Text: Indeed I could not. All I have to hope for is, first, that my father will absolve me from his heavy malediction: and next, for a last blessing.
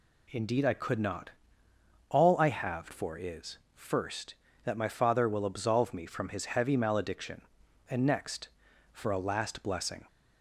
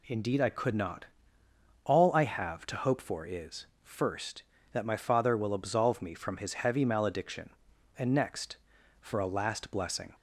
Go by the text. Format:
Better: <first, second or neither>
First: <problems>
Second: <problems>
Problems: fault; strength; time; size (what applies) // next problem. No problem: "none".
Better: second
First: skips "to hope"; at 2.9 s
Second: none